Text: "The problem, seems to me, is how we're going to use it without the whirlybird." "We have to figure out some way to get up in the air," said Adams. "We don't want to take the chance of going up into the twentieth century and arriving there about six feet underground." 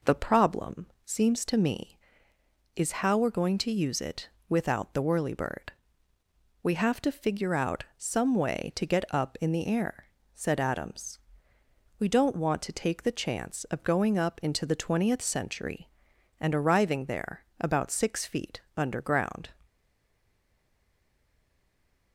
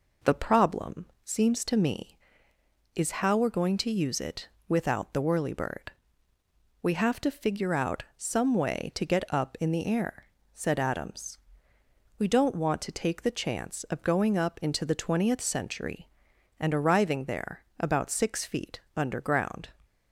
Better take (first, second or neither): second